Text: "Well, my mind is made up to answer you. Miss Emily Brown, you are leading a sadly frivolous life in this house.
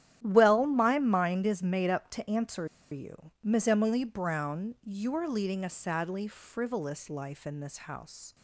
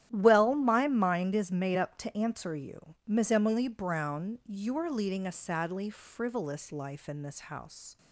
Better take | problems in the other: second | starts louder than the rest; strong; until 1.2 s; 11 dB; strong in the second // pauses between "answer" and "you"; slight; at 2.6 s; 0.23 s long

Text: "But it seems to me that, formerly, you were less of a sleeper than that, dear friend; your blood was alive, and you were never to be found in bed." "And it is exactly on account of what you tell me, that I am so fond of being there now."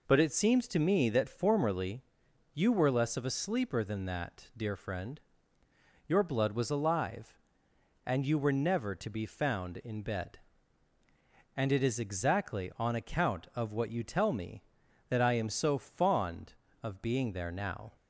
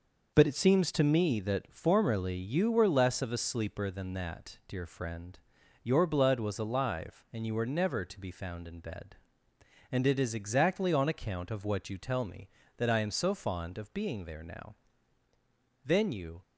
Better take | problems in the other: first | goes on to say "Then you"; from 15.8 s on; 0.56 s long

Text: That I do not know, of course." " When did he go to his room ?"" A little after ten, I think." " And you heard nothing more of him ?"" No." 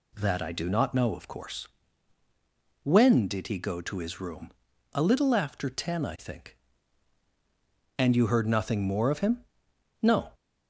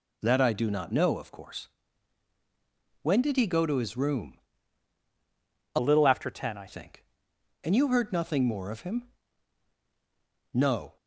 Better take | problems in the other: first | changes voice from "little" to "I"; from 5.7 to 6.6 s; 0.9 s long

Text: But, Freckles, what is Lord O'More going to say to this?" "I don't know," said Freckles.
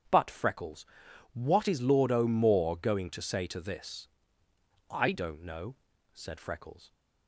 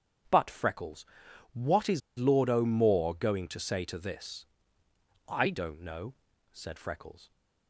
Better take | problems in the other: first | starts louder than the rest; strong; until 1.7 s; 8.5 dB; strong in the first // pauses between "is" and "Lord"; slight; at 2.0 s; 0.18 s long

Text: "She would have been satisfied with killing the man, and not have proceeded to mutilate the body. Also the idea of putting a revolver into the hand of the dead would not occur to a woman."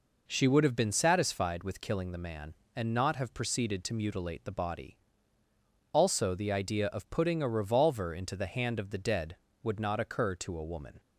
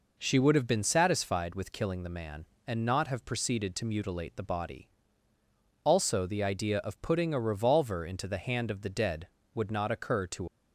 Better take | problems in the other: first | stops before "a woman"; at 10.4 s

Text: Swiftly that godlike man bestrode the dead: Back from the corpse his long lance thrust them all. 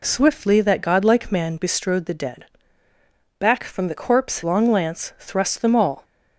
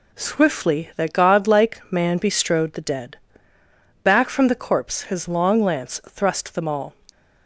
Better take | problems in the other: second | skips "his"; at 4.4 s

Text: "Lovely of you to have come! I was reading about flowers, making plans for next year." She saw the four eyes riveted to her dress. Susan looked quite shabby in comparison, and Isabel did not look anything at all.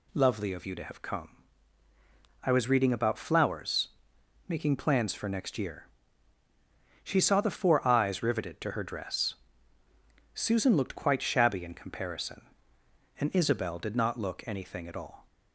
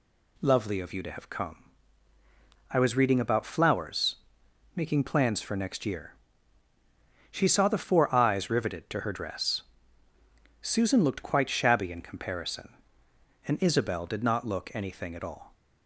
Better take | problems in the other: neither | none

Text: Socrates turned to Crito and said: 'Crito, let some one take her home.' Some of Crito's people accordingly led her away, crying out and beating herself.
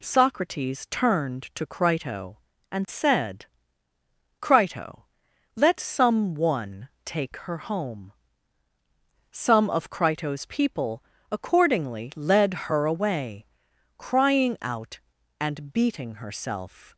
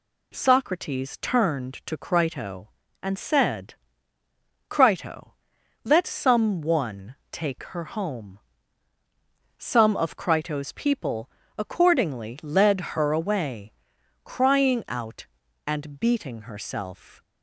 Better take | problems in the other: neither | pauses between "one" and "take"; slight; the same in both // pauses between "people" and "accordingly"; slight; the same in both

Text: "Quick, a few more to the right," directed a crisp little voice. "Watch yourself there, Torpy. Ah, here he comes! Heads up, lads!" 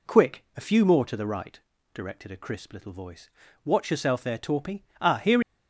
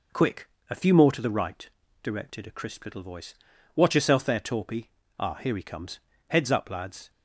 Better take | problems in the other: second | stops before "he comes Heads up lads"; at 5.4 s

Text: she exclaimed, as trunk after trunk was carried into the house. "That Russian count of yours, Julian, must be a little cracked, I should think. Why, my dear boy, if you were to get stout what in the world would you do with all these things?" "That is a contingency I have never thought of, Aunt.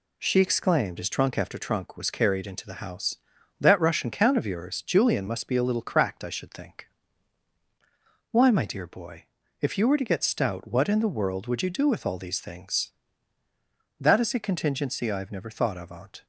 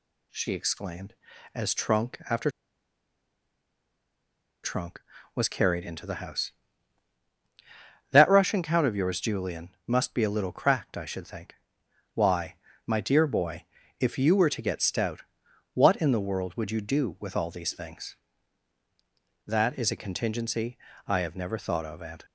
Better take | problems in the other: first | pauses between "after" and "trunk"; strong; at 2.4 s; 2.1 s long // pauses between "stout" and "what"; noticeable; at 15.2 s; 0.52 s long // pauses between "contingency" and "I"; slight; at 20.7 s; 0.30 s long

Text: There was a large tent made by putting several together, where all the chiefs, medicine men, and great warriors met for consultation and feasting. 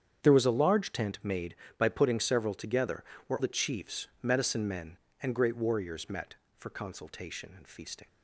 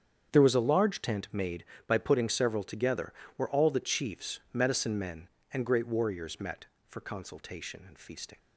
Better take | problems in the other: second | starts louder than the rest; strong; until 1.2 s; 8 dB; strong in the second // skips "all"; at 3.3 s

